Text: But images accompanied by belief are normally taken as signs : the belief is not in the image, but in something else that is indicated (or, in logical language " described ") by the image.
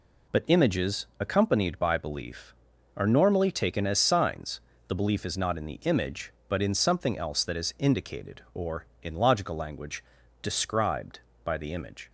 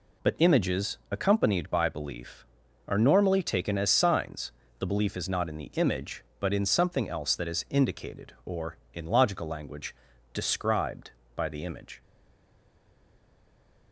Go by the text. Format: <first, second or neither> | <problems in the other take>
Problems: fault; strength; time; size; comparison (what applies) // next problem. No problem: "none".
first | stays silent after the last word; noticeable; from 12.0 s on; 1.9 s long